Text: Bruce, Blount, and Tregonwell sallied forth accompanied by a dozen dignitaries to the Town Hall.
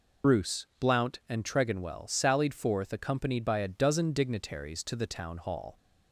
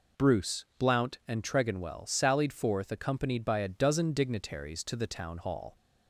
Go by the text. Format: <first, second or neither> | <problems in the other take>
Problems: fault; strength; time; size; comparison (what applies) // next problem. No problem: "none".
second | loses the start of "Bruce"; at 0.2 s; 65 ms